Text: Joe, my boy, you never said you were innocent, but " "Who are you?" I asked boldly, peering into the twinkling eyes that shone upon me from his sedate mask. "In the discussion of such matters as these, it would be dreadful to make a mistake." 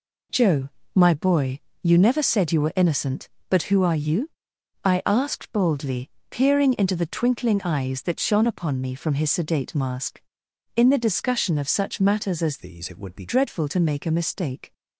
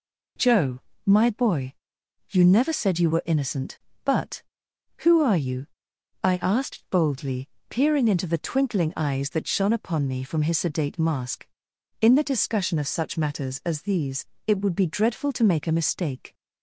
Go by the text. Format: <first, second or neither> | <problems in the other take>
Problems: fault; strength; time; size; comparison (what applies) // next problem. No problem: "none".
second | changes voice from "these" to "be"; from 12.6 to 13.2 s; 0.6 s long